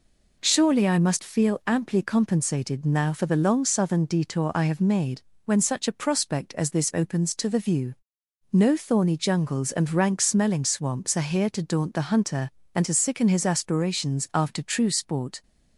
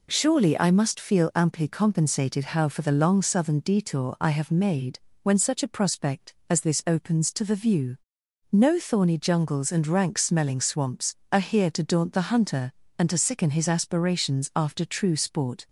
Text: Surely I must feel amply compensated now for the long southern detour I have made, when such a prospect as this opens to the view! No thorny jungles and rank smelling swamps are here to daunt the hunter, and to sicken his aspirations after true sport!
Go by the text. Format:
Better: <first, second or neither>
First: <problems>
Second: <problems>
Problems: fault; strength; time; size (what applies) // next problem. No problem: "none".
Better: first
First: none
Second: says "how" for "now"; at 2.4 s